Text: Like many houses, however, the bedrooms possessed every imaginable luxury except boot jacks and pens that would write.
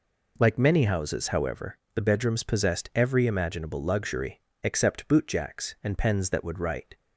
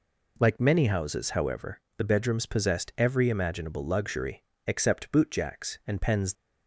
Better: first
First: pauses between "luxury" and "except"; slight; at 4.4 s; 0.21 s long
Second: pauses between "luxury" and "except"; slight; at 4.4 s; 0.22 s long // stops before "that would write"; at 6.3 s

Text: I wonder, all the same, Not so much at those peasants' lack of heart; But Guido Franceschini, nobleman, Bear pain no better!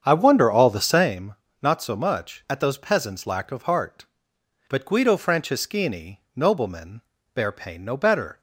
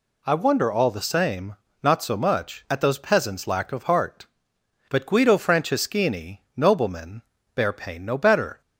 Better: second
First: starts louder than the rest; strong; until 1.1 s; 7.5 dB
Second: none

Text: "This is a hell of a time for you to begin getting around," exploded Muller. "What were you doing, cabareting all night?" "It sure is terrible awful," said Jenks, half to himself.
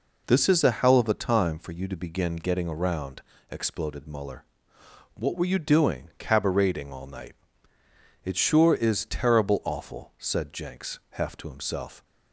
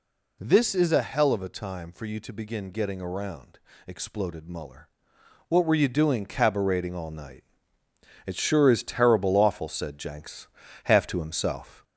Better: first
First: none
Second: gets louder; slight; throughout; 2 dB

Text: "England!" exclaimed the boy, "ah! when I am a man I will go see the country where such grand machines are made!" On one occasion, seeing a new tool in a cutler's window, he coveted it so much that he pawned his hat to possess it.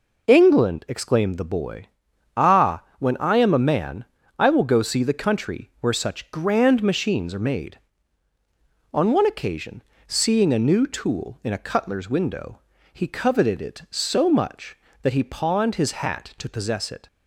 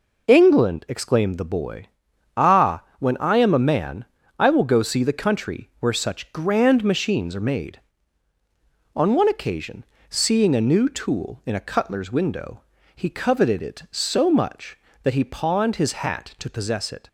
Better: neither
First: pauses between "man" and "I"; slight; at 4.0 s; 0.34 s long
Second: pauses between "man" and "I"; slight; at 4.0 s; 0.34 s long

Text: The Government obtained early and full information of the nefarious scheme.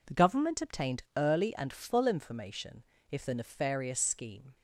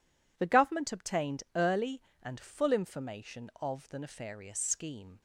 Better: second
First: says "if" for "of"; at 3.1 s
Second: none

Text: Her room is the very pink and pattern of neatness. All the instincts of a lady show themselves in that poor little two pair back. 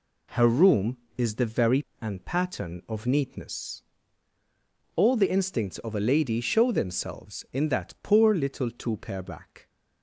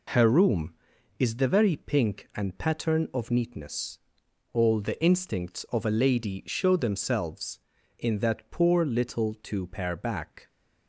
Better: second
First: skips "pink"; at 1.9 s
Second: none

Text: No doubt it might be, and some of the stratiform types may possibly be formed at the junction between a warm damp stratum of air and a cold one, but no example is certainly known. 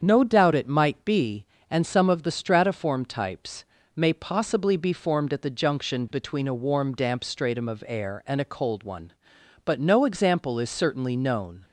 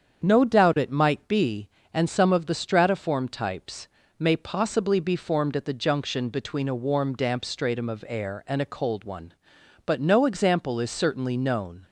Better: neither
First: starts louder than the rest; strong; until 1.0 s; 7.5 dB // pauses between "types" and "may"; slight; at 3.6 s; 0.30 s long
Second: starts louder than the rest; strong; until 1.3 s; 7.5 dB // pauses between "types" and "may"; slight; at 3.8 s; 0.30 s long

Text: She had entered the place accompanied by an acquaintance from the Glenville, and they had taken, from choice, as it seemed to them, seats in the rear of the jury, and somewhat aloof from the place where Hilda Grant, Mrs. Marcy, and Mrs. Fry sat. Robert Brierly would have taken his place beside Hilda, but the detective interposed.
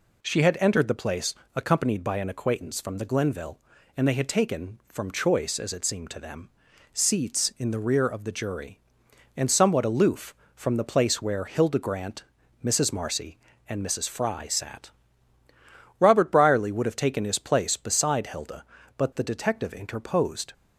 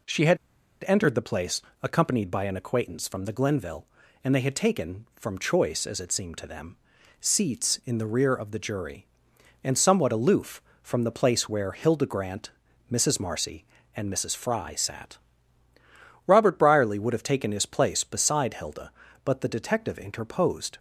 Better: first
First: pauses between "place" and "accompanied"; slight; at 1.3 s; 0.20 s long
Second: pauses between "had" and "entered"; noticeable; at 0.3 s; 0.50 s long // pauses between "place" and "accompanied"; slight; at 1.6 s; 0.20 s long

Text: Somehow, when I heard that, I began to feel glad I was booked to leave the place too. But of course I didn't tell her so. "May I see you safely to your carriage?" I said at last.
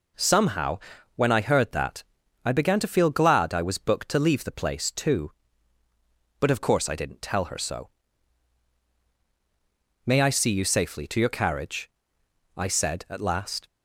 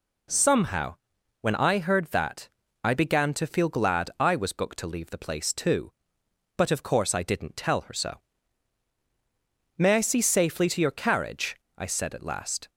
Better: first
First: none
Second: skips "you"; at 10.2 s

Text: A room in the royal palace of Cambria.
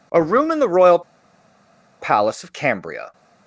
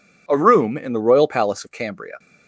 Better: second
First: pauses between "royal" and "palace"; at 1.0 s; 1.0 s long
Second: none

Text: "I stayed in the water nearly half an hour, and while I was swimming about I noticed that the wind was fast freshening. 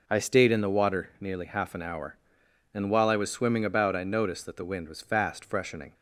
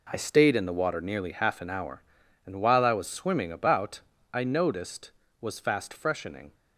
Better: first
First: none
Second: pauses between "about" and "I"; slight; at 3.9 s; 0.32 s long // skips "that the wind"; at 5.2 s

